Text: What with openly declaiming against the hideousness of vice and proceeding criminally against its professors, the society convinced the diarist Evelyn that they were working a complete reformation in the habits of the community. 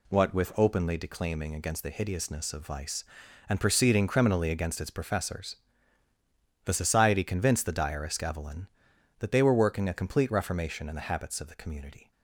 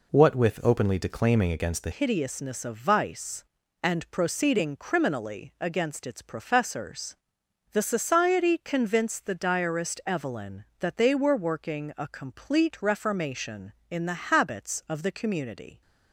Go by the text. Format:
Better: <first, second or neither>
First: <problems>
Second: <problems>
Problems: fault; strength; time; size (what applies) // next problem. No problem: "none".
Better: first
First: none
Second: changes voice at "hideousness"; from 1.9 s on; 13.9 s long